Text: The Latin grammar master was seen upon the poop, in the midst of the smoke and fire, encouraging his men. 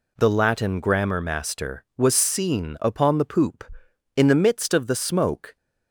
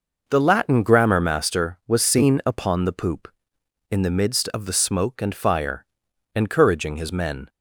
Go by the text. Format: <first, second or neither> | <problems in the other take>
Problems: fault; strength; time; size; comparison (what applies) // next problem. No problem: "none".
second | stops before "and fire encouraging his men"; at 5.5 s